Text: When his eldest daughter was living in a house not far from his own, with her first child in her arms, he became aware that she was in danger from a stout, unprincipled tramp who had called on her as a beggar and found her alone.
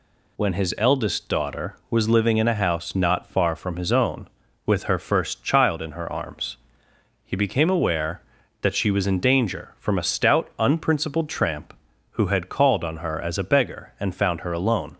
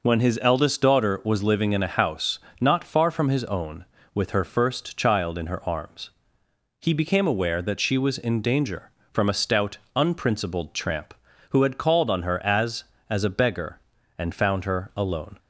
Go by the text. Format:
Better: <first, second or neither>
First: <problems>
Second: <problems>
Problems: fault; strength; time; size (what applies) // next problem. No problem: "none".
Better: first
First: none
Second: pauses between "house" and "not"; slight; at 2.3 s; 0.20 s long // says "as" twice; at 13.1 s